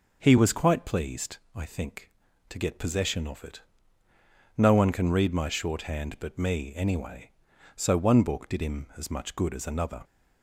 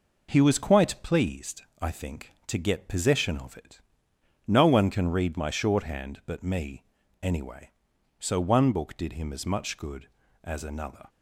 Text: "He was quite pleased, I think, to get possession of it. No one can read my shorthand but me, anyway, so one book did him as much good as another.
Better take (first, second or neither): first